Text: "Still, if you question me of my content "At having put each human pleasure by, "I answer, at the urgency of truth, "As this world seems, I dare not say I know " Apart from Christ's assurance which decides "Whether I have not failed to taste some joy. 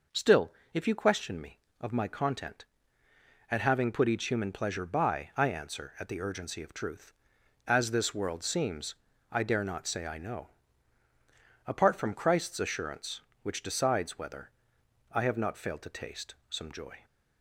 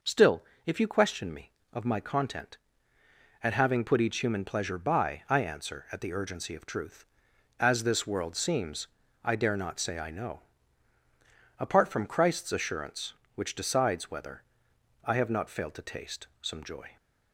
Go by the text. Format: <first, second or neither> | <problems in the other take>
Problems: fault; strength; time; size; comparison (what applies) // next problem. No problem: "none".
neither | pauses between "Whether" and "I"; noticeable; the same in both